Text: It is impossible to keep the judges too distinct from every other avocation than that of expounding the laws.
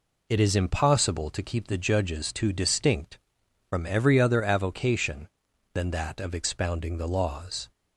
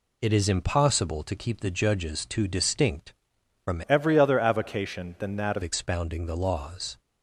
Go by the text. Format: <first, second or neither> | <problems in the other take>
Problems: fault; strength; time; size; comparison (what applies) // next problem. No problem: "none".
first | changes voice from "every" to "of"; from 3.8 to 5.6 s; 1.8 s long